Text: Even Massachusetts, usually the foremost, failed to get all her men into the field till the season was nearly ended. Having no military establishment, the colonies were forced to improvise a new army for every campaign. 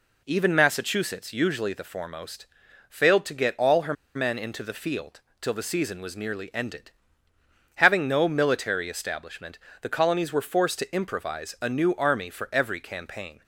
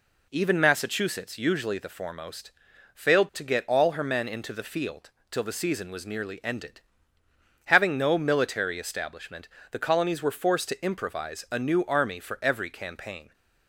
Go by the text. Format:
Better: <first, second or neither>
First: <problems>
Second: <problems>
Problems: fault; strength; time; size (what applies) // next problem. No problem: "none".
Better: second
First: pauses between "her" and "men"; slight; at 3.9 s; 0.22 s long // pauses between "field" and "till"; slight; at 5.2 s; 0.18 s long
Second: pauses between "field" and "till"; slight; at 5.1 s; 0.18 s long